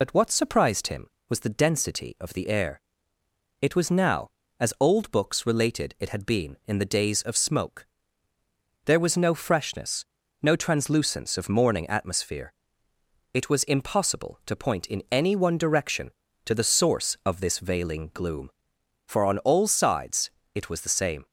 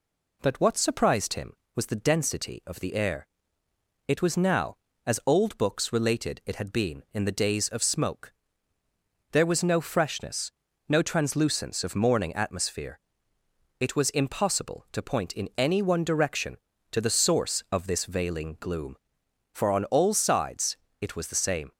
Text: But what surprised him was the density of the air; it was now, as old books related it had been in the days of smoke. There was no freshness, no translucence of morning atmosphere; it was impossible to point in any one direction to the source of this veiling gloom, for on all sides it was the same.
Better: second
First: loses the start of "But"; at 0.0 s; 60 ms // pauses between "sides" and "it"; slight; at 20.3 s; 0.24 s long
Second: pauses between "sides" and "it"; slight; at 20.7 s; 0.24 s long

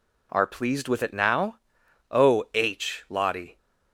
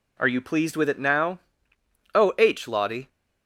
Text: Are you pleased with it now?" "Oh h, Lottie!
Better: second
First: skips "you"; at 0.4 s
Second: none

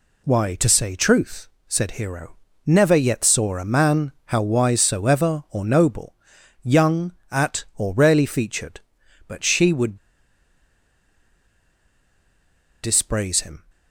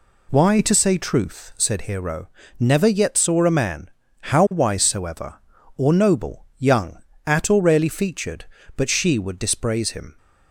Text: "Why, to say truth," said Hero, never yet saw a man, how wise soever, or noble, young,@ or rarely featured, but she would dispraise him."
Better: second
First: pauses between "would" and "dispraise"; strong; at 9.9 s; 2.8 s long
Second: none

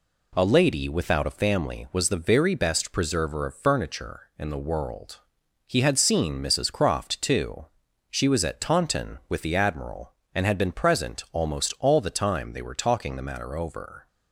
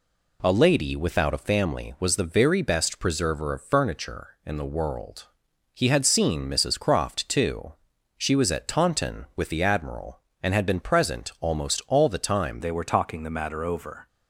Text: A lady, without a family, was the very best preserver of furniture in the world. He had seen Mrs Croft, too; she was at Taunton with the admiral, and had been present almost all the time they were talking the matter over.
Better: first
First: none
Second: changes voice at "they"; from 12.6 s on; 1.4 s long

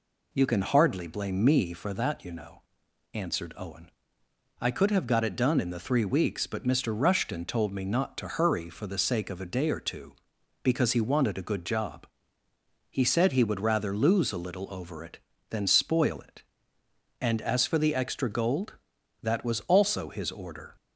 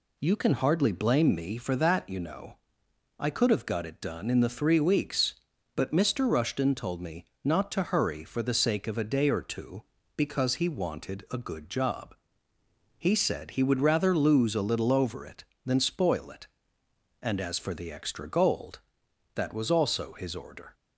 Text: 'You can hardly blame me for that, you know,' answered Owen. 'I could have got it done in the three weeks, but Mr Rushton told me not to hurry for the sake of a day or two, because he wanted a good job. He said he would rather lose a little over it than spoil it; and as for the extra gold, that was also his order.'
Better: first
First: none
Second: skips "answered Owen"; at 2.8 s // pauses between "me" and "not"; slight; at 7.2 s; 0.20 s long

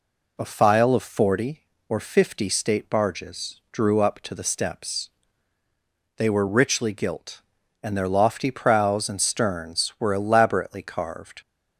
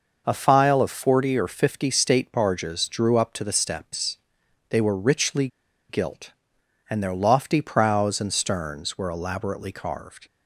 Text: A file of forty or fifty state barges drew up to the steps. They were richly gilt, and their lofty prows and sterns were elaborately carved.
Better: first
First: none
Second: pauses between "richly" and "gilt"; at 5.4 s; 0.42 s long

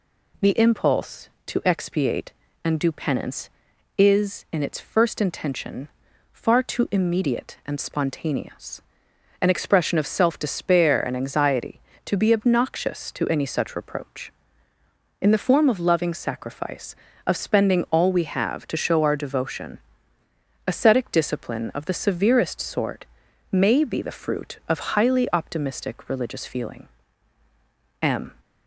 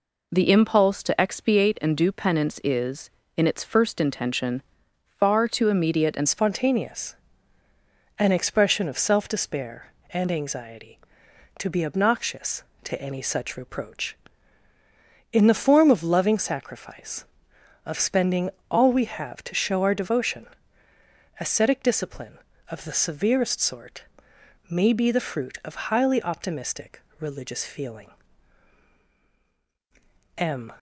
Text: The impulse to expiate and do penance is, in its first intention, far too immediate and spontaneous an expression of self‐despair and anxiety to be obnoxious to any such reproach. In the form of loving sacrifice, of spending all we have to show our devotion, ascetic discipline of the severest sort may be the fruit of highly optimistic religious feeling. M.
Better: first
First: pauses between "spontaneous" and "an"; noticeable; at 8.8 s; 0.60 s long // pauses between "sort" and "may"; noticeable; at 23.0 s; 0.46 s long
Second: changes voice at "spontaneous"; from 6.2 s on; 24.5 s long // pauses between "spontaneous" and "an"; at 7.1 s; 1.0 s long // pauses between "spending" and "all"; slight; at 18.5 s; 0.18 s long // pauses between "sort" and "may"; noticeable; at 24.0 s; 0.66 s long // pauses between "optimistic" and "religious"; slight; at 27.0 s; 0.18 s long

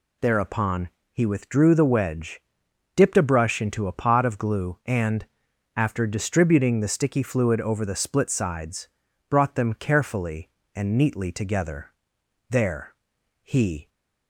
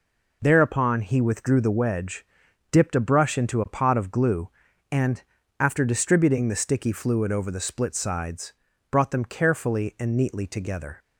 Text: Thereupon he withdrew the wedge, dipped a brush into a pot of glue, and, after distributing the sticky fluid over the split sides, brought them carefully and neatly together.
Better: second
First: pauses between "Thereupon" and "he"; slight; at 0.8 s; 0.24 s long // goes on to say "There he"; from 12.5 s on; 1.3 s long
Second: none

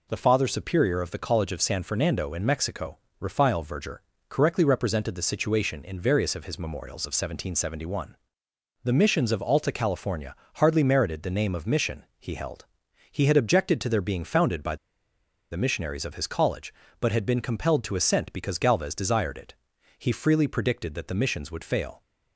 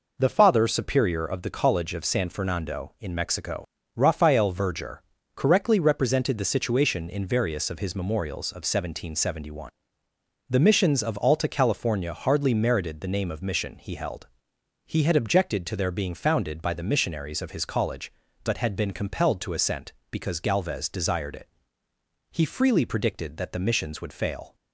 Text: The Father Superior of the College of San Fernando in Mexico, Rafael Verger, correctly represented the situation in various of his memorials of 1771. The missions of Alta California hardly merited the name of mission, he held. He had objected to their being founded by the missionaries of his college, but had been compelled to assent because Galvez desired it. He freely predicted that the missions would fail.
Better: second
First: pauses between "California" and "hardly"; slight; at 10.3 s; 0.22 s long // pauses between "by" and "the"; noticeable; at 14.7 s; 0.75 s long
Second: none

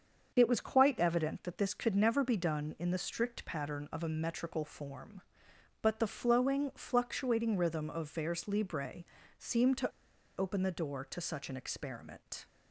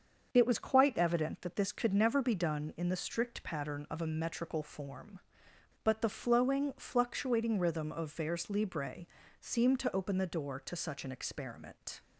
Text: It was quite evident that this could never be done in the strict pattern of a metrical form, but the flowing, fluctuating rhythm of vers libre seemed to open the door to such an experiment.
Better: second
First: starts louder than the rest; until 1.3 s; 7 dB // pauses between "libre" and "seemed"; slight; at 9.0 s; 0.32 s long // pauses between "to" and "open"; noticeable; at 9.9 s; 0.47 s long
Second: starts louder than the rest; until 1.3 s; 7 dB // pauses between "libre" and "seemed"; slight; at 9.0 s; 0.32 s long

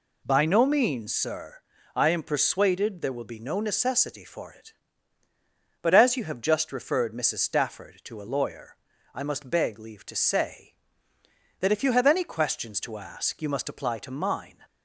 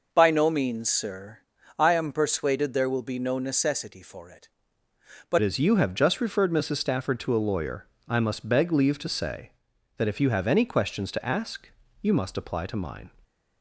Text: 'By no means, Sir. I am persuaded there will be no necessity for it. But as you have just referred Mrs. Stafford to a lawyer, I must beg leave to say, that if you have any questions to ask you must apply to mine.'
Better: first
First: none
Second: changes voice at "as"; from 5.4 s on; 7.7 s long // pauses between "ask" and "you"; slight; at 11.6 s; 0.32 s long

